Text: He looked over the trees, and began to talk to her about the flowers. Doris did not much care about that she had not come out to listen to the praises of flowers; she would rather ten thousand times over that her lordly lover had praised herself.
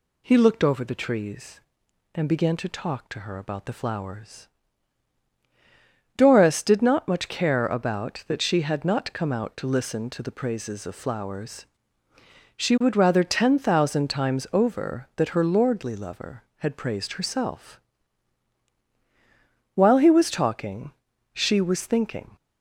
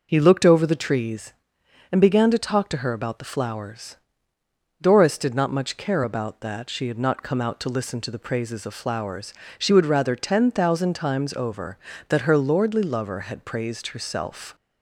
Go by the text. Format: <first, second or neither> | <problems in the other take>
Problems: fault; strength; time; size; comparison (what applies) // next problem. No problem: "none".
second | goes on to say "While he was talking she was thinking"; strong; from 19.7 s on; 2.6 s long